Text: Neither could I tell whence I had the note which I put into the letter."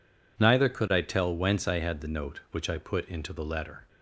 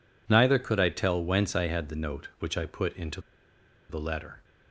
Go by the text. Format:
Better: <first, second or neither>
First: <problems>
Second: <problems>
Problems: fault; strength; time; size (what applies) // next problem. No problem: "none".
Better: first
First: none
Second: pauses between "into" and "the"; noticeable; at 3.1 s; 0.69 s long